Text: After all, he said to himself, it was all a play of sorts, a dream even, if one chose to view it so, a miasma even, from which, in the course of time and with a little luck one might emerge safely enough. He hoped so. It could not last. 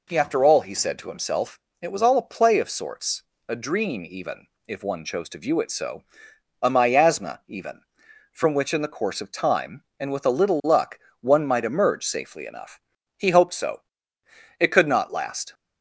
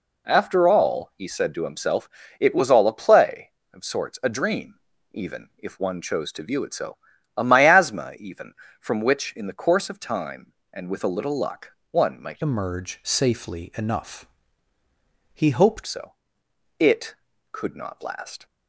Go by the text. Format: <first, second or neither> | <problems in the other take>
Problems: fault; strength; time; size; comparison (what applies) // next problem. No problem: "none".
first | pauses between "dream" and "even"; at 4.7 s; 0.38 s long // pauses between "luck" and "one"; slight; at 11.6 s; 0.20 s long; slight in the first // changes voice from "emerge" to "hoped"; from 12.4 to 15.8 s; 3.4 s long